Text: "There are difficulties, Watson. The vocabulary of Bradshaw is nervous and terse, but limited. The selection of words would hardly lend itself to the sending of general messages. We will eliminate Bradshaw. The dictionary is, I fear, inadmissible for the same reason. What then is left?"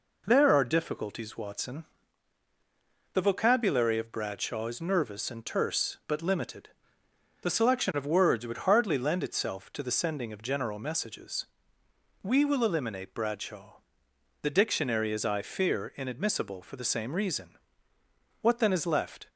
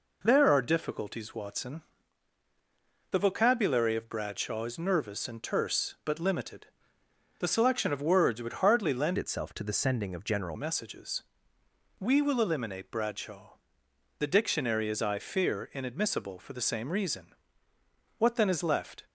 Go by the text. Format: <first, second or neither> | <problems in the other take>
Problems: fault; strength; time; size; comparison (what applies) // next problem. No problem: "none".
first | changes voice from "itself" to "general"; from 9.1 to 10.5 s; 1.4 s long